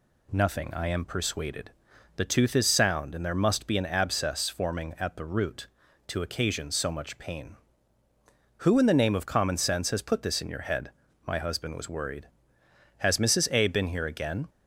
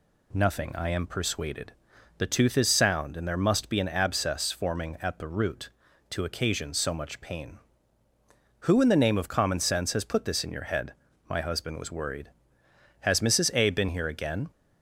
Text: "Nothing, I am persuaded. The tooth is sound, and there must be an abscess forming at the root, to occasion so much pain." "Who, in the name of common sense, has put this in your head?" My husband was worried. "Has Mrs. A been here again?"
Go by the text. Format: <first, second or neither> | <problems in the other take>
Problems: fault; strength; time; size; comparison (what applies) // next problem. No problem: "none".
neither | none